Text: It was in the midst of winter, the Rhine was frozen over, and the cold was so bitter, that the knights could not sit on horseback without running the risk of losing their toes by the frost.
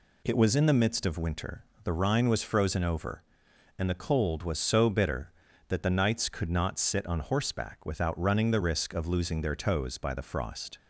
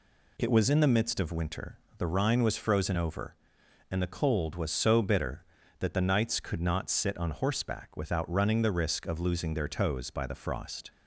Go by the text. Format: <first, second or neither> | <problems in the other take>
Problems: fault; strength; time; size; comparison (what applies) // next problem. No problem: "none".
neither | none